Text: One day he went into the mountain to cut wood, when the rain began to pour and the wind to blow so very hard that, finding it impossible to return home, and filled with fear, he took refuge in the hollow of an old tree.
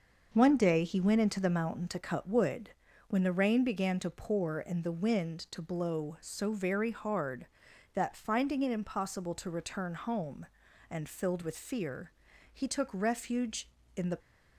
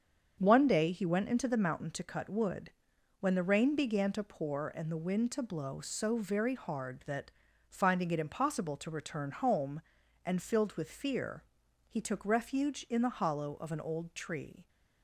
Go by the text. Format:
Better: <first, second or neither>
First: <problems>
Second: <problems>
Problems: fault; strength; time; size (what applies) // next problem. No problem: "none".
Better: second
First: starts louder than the rest; until 1.3 s; 6 dB // stops before "hollow of an old tree"; at 14.1 s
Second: starts louder than the rest; strong; until 1.3 s; 7 dB